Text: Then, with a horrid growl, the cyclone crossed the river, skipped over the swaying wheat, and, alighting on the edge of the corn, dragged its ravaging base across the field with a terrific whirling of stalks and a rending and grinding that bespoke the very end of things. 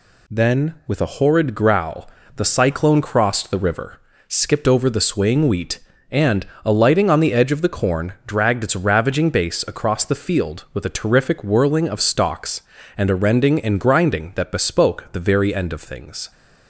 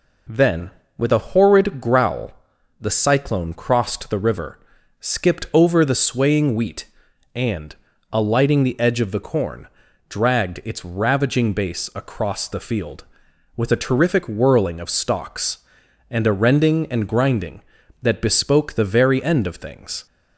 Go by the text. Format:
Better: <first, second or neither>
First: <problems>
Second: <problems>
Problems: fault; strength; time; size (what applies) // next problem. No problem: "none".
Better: first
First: none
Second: skips "on"; at 8.6 s